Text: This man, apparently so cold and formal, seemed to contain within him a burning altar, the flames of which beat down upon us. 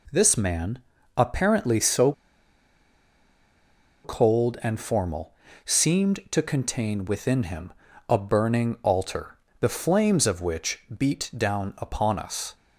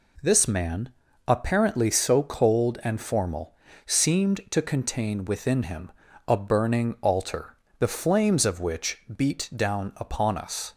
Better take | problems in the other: second | pauses between "so" and "cold"; strong; at 2.1 s; 1.9 s long // pauses between "him" and "a"; at 7.7 s; 0.38 s long; also in the second

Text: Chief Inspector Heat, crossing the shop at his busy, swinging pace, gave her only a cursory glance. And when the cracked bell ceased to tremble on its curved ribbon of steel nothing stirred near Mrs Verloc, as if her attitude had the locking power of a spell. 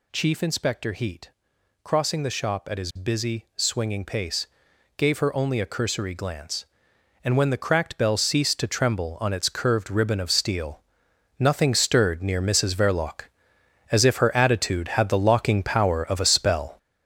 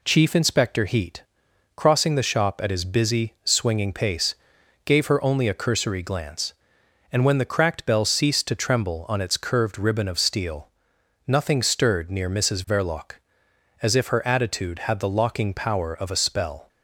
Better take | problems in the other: second | gets louder; strong; throughout; 7.5 dB // pauses between "steel" and "nothing"; noticeable; at 10.7 s; 0.60 s long; noticeable in the second

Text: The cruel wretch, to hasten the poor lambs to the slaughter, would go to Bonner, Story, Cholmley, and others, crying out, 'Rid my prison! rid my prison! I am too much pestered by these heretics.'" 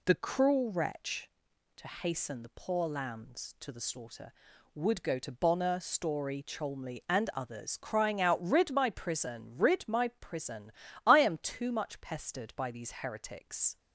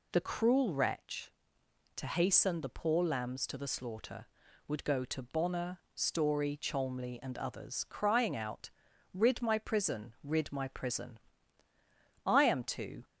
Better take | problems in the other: first | stops before "much pestered by these heretics"; at 13.0 s

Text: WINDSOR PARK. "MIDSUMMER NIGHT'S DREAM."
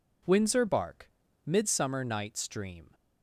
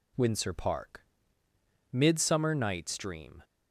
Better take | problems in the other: second | says "Bark" for "PARK"; at 0.6 s

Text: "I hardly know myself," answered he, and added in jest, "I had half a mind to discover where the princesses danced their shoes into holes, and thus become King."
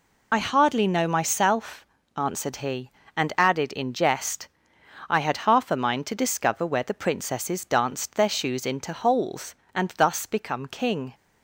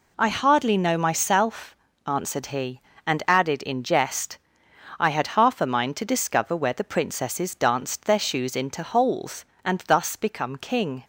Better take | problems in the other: second | loses the start of "I"; at 0.3 s; 55 ms

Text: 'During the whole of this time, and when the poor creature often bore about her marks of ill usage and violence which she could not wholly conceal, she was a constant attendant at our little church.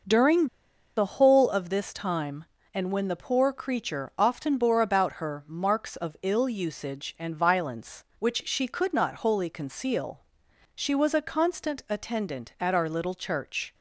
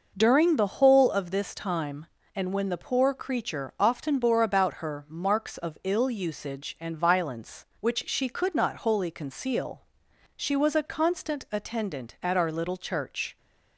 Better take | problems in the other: second | pauses between "During" and "the"; noticeable; at 0.4 s; 0.49 s long

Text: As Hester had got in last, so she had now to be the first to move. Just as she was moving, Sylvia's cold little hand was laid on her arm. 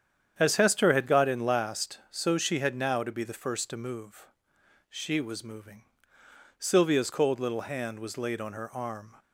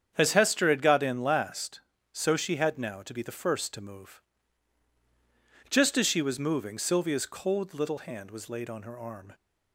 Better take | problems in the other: second | starts louder than the rest; strong; until 1.3 s; 8.5 dB; strong in the second // skips "Just as"; at 4.5 s

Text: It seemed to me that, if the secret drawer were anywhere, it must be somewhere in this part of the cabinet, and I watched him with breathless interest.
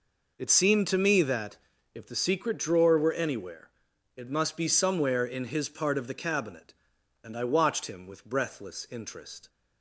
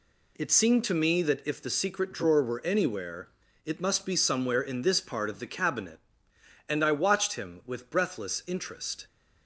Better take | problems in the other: second | says "his" for "this"; at 5.4 s

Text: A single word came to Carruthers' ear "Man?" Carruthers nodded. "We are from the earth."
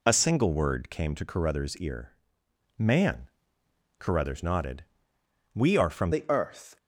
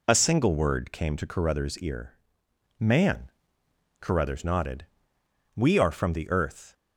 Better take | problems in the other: second | pauses between "ear" and "Man"; noticeable; at 2.1 s; 0.62 s long; noticeable in the second // changes voice at "the"; from 6.1 s on; 0.6 s long

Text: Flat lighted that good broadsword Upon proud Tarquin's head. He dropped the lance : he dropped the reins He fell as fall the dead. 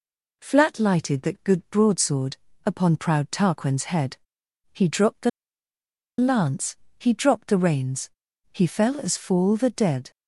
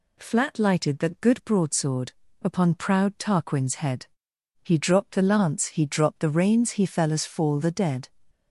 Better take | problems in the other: second | pauses between "broadsword" and "Upon"; slight; at 2.3 s; 0.30 s long; slight in the second // pauses between "the" and "lance"; noticeable; at 5.2 s; 0.88 s long // pauses between "reins" and "He"; at 8.0 s; 0.44 s long

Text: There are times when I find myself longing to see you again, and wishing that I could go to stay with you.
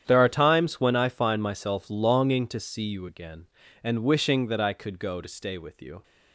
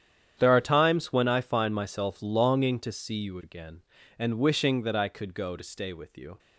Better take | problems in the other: neither | starts louder than the rest; strong; the same in both

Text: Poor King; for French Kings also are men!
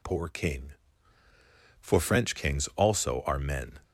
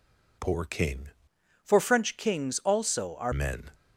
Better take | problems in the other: first | changes voice from "for" to "are"; from 1.6 to 3.3 s; 1.7 s long

